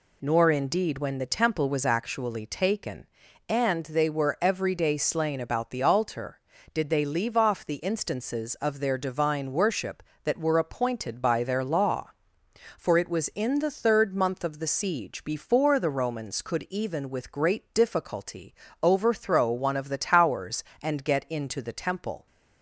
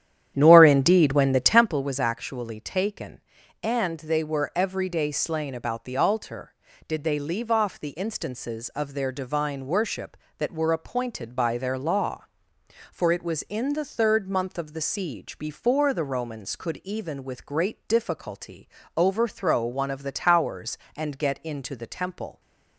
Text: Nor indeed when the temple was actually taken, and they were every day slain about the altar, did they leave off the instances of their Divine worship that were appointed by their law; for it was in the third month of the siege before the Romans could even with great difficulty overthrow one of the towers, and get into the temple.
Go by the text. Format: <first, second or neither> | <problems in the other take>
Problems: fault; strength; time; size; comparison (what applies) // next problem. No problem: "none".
first | starts louder than the rest; strong; until 1.8 s; 10.5 dB // pauses between "difficulty" and "overthrow"; slight; at 18.6 s; 0.28 s long; slight in the first